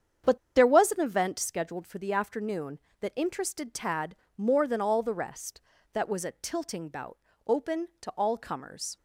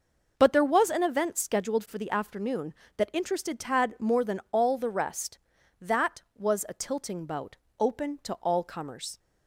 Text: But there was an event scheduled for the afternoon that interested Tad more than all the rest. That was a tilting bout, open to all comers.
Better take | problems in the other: second | starts louder than the rest; strong; until 1.4 s; 8 dB // pauses between "But" and "there"; slight; at 0.3 s; 0.18 s long // pauses between "Tad" and "more"; slight; at 4.1 s; 0.20 s long

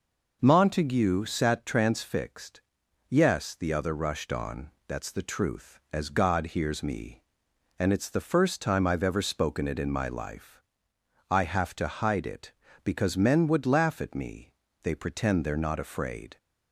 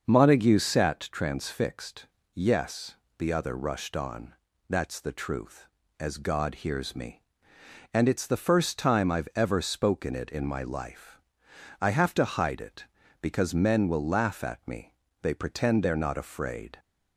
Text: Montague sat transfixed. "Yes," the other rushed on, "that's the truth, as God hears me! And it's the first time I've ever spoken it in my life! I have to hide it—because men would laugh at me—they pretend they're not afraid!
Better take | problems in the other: first | starts louder than the rest; until 1.0 s; 6 dB // says "will" for "would"; at 13.8 s

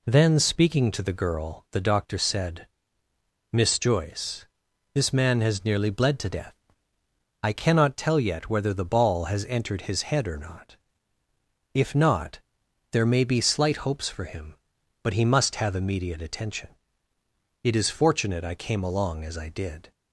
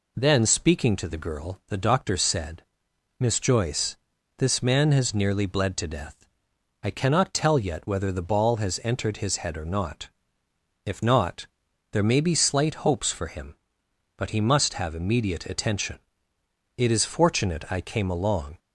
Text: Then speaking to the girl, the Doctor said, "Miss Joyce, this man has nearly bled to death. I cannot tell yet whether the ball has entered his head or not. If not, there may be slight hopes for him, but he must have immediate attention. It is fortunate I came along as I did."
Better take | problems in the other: first | stops before "as I did"; at 18.5 s

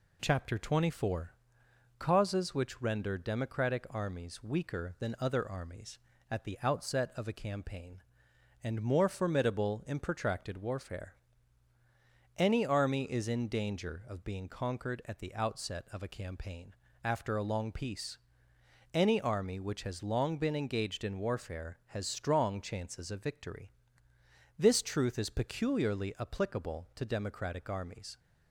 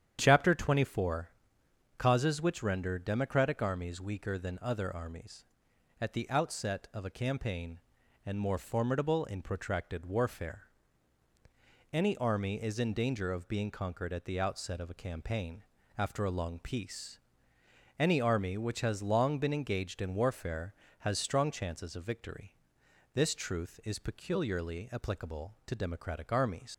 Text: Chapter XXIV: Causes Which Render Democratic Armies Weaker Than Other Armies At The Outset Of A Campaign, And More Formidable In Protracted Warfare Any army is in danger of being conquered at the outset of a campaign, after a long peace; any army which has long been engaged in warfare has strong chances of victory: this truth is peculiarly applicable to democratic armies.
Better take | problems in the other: first | starts louder than the rest; strong; until 1.2 s; 9.5 dB // pauses between "Warfare" and "Any"; strong; at 10.6 s; 1.2 s long; also in the first // leaves "armies" unfinished; at 26.7 s; 90 ms

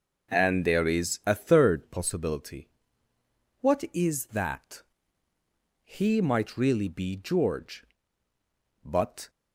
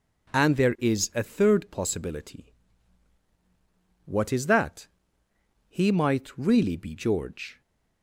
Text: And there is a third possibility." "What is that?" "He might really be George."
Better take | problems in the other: second | starts louder than the rest; noticeable; until 1.3 s; 6 dB // goes on to say "But"; slight; from 8.8 s on; 0.46 s long

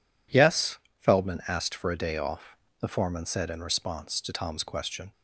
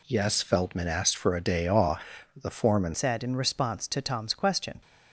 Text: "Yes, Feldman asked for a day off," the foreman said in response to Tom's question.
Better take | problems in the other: first | changes voice at "said"; from 2.9 s on; 1.9 s long

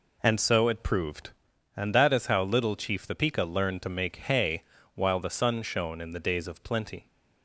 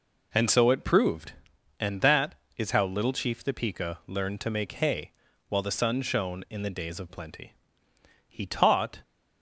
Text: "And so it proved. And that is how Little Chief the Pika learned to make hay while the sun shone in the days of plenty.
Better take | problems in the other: first | pauses between "hay" and "while"; slight; at 5.1 s; 0.36 s long; slight in the first // goes on to say "He taught"; noticeable; from 8.2 s on; 0.74 s long

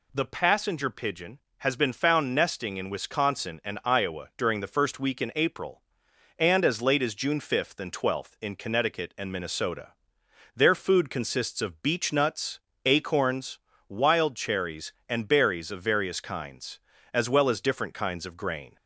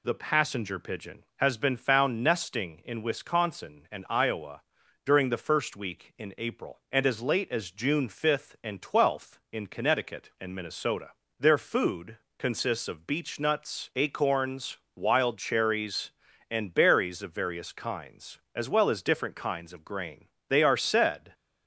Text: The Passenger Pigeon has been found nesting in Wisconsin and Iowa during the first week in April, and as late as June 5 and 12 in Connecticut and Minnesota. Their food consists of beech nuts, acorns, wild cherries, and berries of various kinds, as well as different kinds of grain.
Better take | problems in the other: first | pauses between "Iowa" and "during"; at 4.6 s; 0.42 s long // pauses between "food" and "consists"; slight; at 12.1 s; 0.20 s long // goes on to say "They are said"; noticeable; from 20.4 s on; 0.84 s long

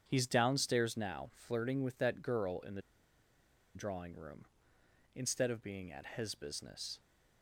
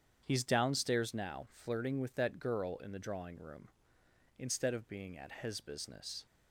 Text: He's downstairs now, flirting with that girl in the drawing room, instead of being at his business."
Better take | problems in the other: second | starts louder than the rest; strong; until 1.0 s; 8 dB; strong in the second // pauses between "the" and "drawing"; noticeable; at 2.8 s; 0.94 s long

